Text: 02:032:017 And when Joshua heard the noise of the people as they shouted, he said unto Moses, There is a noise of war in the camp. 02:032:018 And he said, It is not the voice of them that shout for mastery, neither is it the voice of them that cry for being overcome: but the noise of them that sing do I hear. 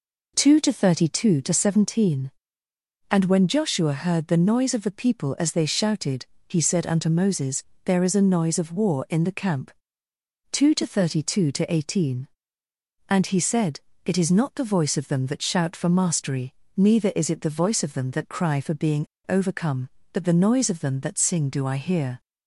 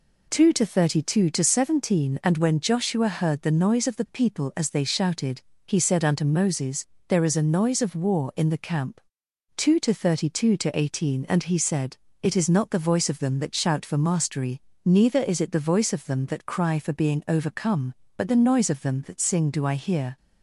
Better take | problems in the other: second | pauses between "being" and "overcome"; slight; at 19.0 s; 0.23 s long

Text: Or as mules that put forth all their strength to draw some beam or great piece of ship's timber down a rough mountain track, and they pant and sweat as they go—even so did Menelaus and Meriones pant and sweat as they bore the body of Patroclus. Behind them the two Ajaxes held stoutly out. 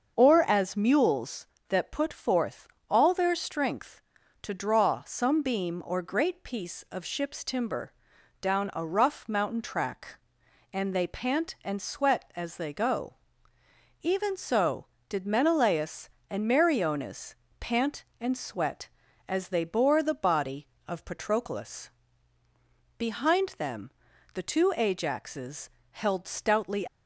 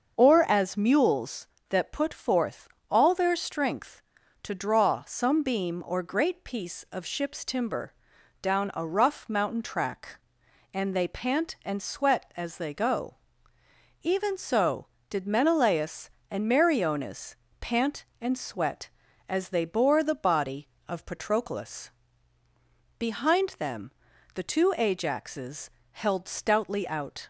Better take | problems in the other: second | starts louder than the rest; until 1.2 s; 6.5 dB; also in the second // pauses between "forth" and "all"; slight; at 2.6 s; 0.20 s long; slight in the second // pauses between "timber" and "down"; noticeable; at 7.9 s; 0.48 s long; noticeable in the second // pauses between "Meriones" and "pant"; slight; at 17.3 s; 0.24 s long; slight in the second // pauses between "them" and "the"; at 23.9 s; 0.44 s long; also in the second // pauses between "Ajaxes" and "held"; slight; at 25.7 s; 0.20 s long; slight in the second // stops before "out"; at 26.8 s

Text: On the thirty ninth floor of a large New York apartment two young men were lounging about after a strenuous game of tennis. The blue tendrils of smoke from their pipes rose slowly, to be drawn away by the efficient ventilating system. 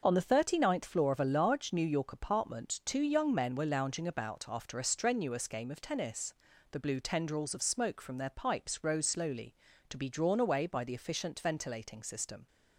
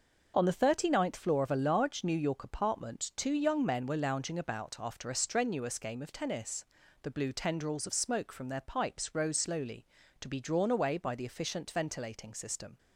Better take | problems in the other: neither | none

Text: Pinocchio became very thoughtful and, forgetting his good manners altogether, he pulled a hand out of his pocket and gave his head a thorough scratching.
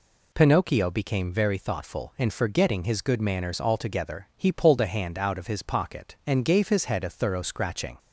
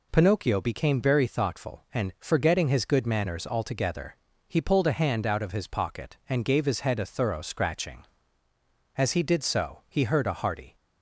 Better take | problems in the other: first | goes on to say "As he did so he heard a hearty"; strong; from 8.9 s on; 1.7 s long

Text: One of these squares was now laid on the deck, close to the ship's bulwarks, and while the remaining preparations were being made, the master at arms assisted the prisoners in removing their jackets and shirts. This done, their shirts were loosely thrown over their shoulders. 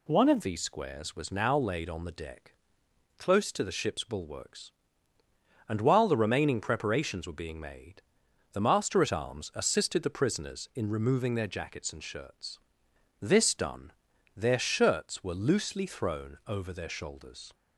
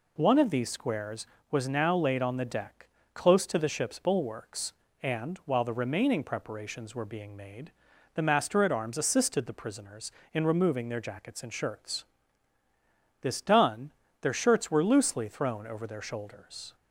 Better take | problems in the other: second | changes voice at "these"; from 0.4 s on; 17.1 s long

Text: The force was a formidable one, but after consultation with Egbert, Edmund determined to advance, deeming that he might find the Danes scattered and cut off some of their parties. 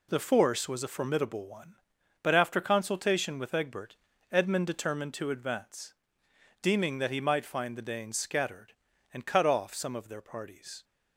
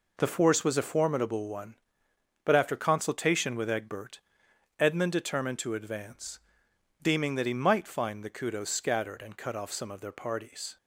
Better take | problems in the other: first | says "Kudos" for "Danes"; at 8.3 s

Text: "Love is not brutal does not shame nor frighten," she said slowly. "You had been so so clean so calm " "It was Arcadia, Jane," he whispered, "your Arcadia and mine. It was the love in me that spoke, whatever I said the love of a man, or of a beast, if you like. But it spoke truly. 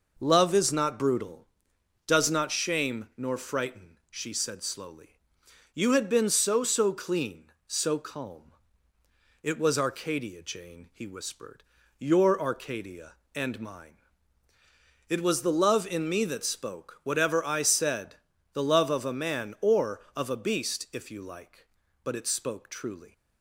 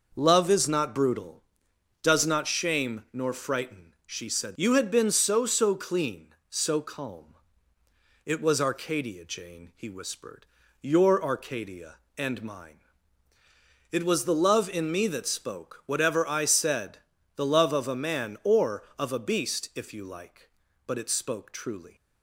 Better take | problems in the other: first | skips "slowly"; at 4.5 s // pauses between "said" and "the"; at 16.9 s; 0.40 s long; also in the first

